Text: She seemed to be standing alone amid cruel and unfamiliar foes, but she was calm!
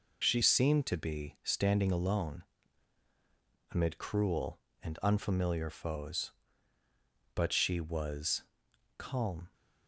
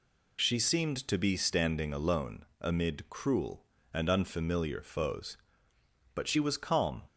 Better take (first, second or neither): second